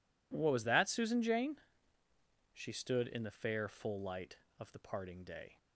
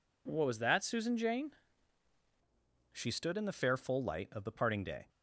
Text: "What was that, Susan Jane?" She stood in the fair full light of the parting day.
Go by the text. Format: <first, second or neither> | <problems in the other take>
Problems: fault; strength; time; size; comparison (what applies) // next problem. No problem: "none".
first | changes voice at "She"; from 2.9 s on; 2.1 s long